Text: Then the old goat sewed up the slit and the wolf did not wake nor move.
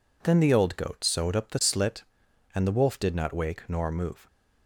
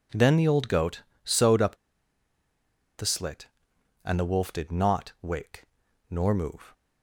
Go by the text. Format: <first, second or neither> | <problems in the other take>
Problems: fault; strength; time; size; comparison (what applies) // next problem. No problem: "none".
first | pauses between "goat" and "sewed"; slight; at 1.0 s; 0.22 s long // pauses between "up" and "the"; at 1.7 s; 1.2 s long // pauses between "wake" and "nor"; noticeable; at 5.6 s; 0.46 s long